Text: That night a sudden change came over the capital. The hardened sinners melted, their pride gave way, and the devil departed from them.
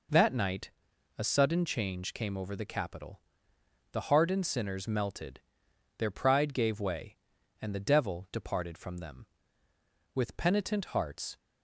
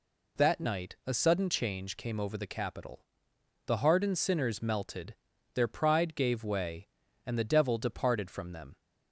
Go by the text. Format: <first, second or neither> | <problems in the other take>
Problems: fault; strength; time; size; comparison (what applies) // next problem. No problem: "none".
second | pauses between "night" and "a"; noticeable; at 0.7 s; 0.46 s long // goes on to say "With penitent hearts"; noticeable; from 10.1 s on; 1.2 s long